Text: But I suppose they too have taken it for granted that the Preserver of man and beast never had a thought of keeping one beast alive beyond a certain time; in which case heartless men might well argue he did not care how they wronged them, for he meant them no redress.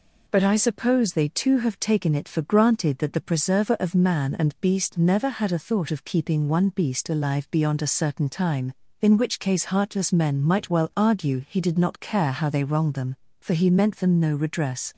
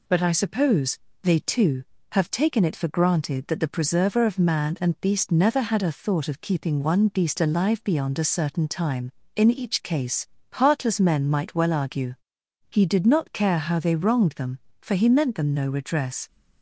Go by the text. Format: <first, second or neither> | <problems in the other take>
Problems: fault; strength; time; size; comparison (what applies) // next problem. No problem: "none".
first | pauses between "suppose" and "they"; slight; at 0.9 s; 0.22 s long // says "each" for "which"; at 9.4 s // pauses between "case" and "heartless"; slight; at 10.2 s; 0.24 s long // pauses between "argue" and "he"; noticeable; at 12.1 s; 0.54 s long